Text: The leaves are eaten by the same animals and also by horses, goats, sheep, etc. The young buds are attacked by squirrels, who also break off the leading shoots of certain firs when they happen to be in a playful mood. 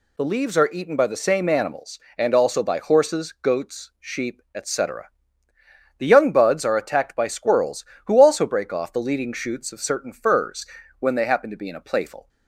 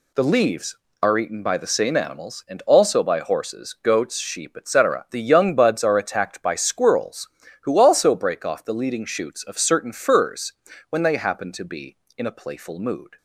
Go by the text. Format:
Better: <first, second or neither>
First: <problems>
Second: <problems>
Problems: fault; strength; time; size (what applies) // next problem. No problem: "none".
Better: second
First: pauses between "firs" and "when"; slight; at 10.6 s; 0.32 s long // stops before "mood"; at 12.2 s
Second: pauses between "firs" and "when"; at 10.5 s; 0.38 s long